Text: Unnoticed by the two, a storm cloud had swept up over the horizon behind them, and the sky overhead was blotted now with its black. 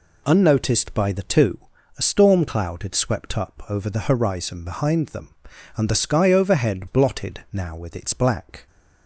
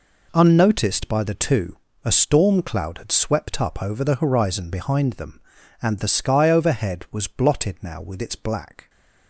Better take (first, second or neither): second